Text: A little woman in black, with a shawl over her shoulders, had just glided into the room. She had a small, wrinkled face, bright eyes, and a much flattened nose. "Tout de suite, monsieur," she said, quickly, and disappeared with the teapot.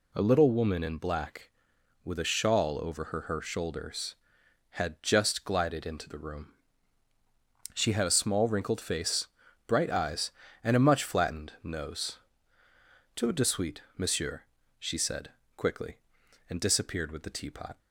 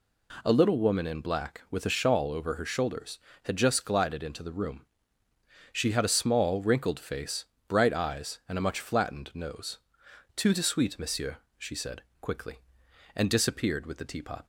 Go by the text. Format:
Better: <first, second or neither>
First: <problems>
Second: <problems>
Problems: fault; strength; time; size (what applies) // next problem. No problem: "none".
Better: second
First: says "her" twice; at 3.2 s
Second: none